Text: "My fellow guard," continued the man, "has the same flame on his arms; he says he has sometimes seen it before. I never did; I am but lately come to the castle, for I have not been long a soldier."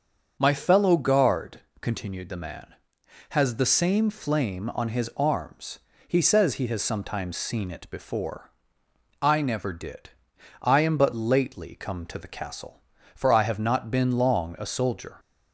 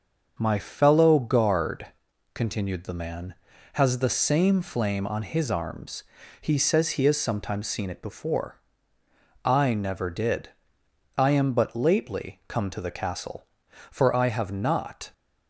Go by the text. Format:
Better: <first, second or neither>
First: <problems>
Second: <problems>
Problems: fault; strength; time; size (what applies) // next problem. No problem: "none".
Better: first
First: none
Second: starts louder than the rest; until 1.3 s; 6.5 dB // stops before "been long a soldier"; at 15.1 s